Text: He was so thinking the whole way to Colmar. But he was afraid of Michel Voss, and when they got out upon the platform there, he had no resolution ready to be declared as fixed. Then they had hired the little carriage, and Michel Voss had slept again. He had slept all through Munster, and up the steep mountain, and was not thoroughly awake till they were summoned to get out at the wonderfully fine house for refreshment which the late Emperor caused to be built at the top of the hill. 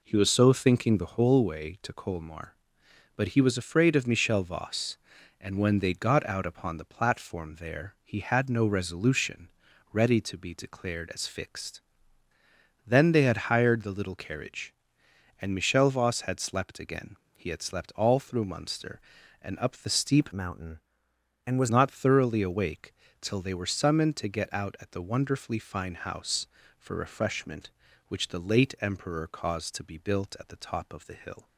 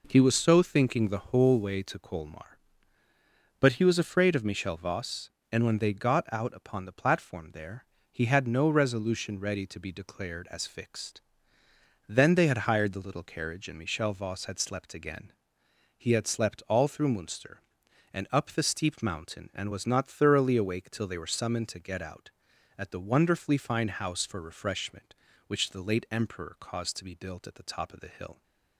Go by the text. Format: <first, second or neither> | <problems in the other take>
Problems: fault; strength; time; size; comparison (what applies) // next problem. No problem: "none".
second | pauses between "resolution" and "ready"; at 9.4 s; 0.42 s long // changes voice from "mountain" to "was"; from 20.3 to 21.6 s; 1.3 s long // pauses between "awake" and "till"; slight; at 22.9 s; 0.28 s long